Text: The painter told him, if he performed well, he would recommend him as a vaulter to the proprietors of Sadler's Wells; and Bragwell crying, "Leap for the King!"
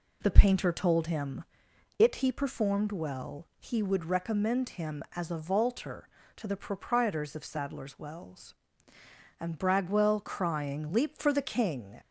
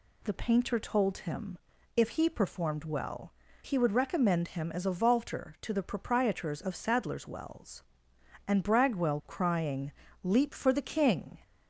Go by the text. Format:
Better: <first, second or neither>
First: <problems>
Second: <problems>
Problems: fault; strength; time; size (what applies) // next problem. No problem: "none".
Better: second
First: says "it" for "if"; at 1.9 s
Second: none